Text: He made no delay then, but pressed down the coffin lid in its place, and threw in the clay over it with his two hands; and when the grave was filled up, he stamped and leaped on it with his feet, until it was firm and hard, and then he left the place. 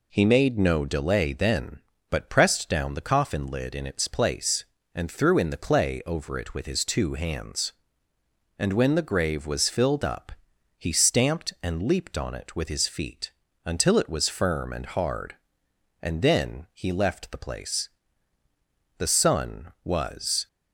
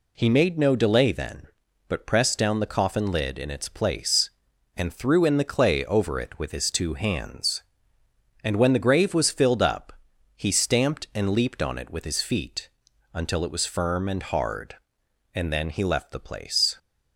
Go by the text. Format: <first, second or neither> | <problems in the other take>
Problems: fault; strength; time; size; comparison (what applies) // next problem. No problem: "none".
second | goes on to say "The sun was"; from 18.9 s on; 1.5 s long